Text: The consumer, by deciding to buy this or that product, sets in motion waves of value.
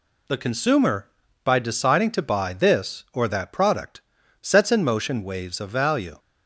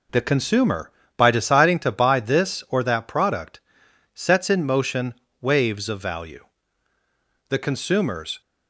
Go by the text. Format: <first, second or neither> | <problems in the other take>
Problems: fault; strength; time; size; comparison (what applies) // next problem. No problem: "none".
first | pauses between "motion" and "waves"; slight; at 5.1 s; 0.26 s long // goes on to say "The consumers"; noticeable; from 7.4 s on; 0.92 s long